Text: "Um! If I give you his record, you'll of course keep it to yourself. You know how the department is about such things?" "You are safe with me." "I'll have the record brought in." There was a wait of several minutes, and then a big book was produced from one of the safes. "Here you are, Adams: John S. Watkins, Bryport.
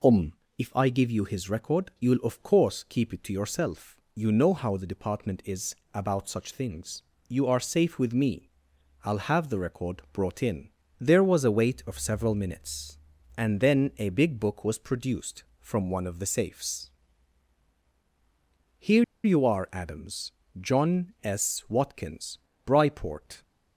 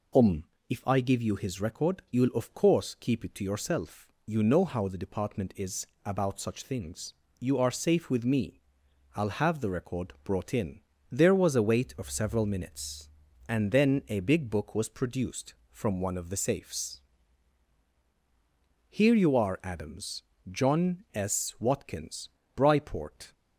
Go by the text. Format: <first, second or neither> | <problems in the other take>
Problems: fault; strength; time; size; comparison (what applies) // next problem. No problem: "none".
second | pauses between "is" and "about"; slight; at 5.7 s; 0.18 s long; slight in the second // pauses between "Here" and "you"; slight; at 19.0 s; 0.19 s long